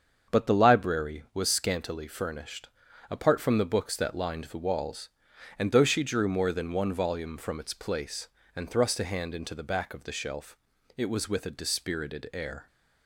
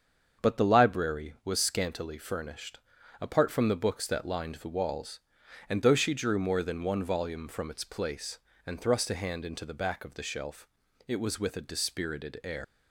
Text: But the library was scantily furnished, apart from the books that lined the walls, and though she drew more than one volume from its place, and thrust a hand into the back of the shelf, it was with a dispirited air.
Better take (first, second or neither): first